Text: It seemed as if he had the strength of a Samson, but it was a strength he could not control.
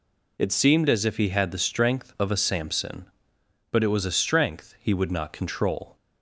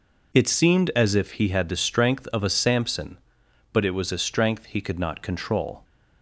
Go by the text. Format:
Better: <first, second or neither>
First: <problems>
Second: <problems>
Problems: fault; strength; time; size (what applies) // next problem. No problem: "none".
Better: second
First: says "would" for "could"; at 4.9 s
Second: none